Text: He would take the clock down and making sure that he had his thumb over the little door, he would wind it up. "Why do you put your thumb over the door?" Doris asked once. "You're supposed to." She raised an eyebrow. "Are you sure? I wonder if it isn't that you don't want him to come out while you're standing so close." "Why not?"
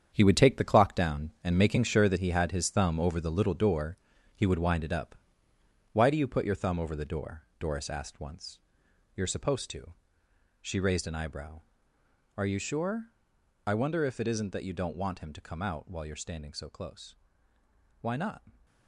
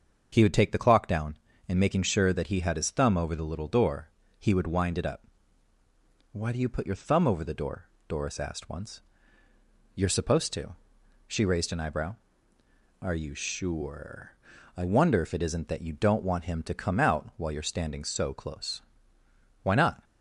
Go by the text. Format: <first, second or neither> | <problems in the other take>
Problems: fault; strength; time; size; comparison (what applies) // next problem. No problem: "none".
second | gets quieter; strong; throughout; 9.5 dB // starts louder than the rest; strong; until 1.1 s; 8 dB; also in the second